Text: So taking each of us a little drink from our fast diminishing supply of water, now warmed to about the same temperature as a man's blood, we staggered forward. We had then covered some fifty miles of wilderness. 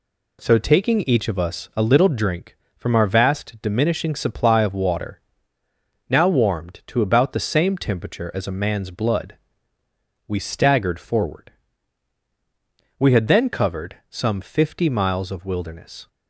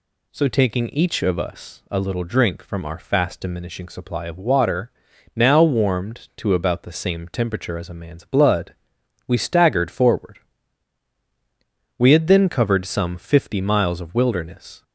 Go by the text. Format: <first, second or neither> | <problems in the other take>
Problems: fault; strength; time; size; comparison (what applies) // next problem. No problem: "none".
second | says "vast" for "fast"; at 3.0 s